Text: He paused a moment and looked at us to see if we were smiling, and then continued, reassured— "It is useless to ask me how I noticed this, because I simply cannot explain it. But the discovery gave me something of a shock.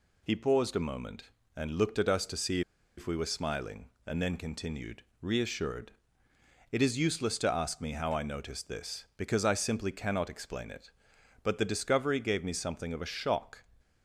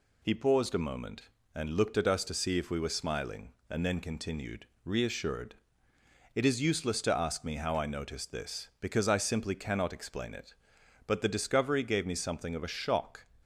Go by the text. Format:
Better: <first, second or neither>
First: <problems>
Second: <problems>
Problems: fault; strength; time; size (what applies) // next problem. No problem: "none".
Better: second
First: pauses between "see" and "if"; at 2.6 s; 0.36 s long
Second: none